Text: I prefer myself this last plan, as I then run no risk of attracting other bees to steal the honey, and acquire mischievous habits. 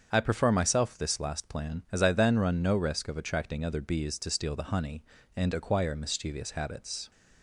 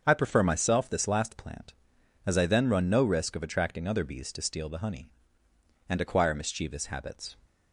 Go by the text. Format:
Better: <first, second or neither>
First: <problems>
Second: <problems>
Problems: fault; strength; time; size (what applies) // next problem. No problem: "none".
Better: first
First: starts louder than the rest; strong; until 1.1 s; 7 dB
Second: starts louder than the rest; until 1.0 s; 6.5 dB // says "plant" for "plan"; at 1.3 s